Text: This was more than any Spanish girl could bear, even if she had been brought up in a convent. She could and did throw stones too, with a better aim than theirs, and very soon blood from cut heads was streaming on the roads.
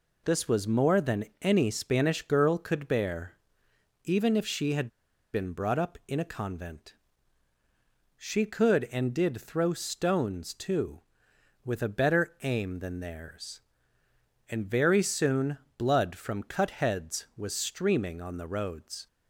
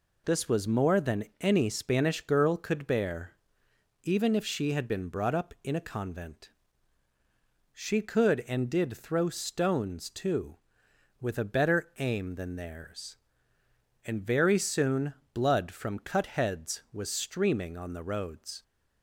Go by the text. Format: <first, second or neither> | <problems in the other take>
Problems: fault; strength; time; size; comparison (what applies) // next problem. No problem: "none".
second | pauses between "than" and "any"; slight; at 1.2 s; 0.16 s long; slight in the second // pauses between "had" and "been"; at 4.8 s; 0.45 s long // pauses between "soon" and "blood"; slight; at 15.5 s; 0.18 s long; slight in the second